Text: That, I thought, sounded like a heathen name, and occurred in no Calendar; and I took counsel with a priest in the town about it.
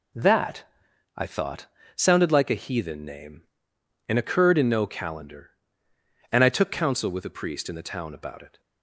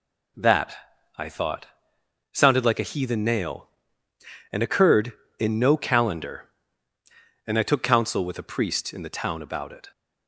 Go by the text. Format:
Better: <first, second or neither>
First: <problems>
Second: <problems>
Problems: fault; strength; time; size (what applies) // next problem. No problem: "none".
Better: first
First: none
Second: says "nail" for "name"; at 3.2 s